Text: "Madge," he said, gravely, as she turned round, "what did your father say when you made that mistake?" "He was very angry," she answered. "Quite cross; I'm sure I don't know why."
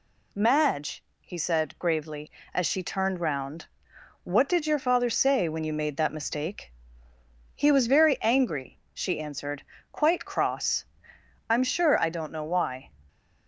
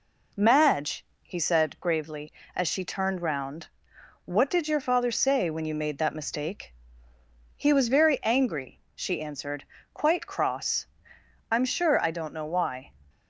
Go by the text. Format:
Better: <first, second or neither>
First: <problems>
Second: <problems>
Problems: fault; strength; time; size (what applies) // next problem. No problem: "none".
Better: first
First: none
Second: starts louder than the rest; slight; until 1.9 s; 3.5 dB